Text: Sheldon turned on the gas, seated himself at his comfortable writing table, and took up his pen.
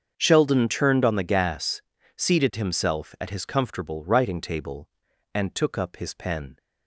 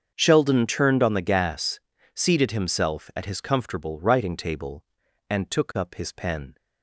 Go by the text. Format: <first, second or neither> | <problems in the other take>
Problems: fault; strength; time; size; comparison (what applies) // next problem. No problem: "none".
neither | starts louder than the rest; strong; the same in both